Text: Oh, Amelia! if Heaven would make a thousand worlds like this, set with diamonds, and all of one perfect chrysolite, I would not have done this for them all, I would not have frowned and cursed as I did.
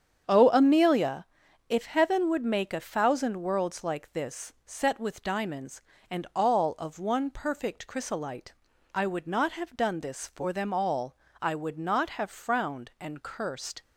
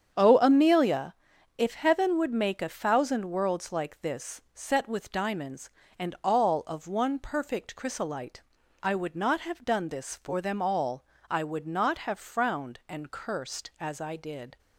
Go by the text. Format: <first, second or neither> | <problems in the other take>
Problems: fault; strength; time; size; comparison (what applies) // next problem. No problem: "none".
second | starts louder than the rest; strong; until 1.7 s; 8 dB; strong in the second // stops before "as I did"; at 13.8 s